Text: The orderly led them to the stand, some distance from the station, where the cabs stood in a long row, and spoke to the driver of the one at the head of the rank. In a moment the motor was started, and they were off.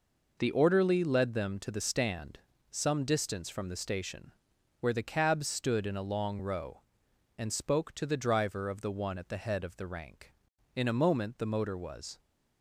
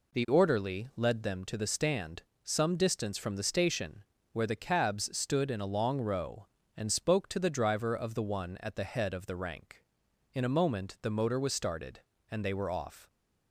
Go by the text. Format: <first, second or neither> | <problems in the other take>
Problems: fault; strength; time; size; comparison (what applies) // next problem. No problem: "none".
second | stops before "started and they were off"; at 12.1 s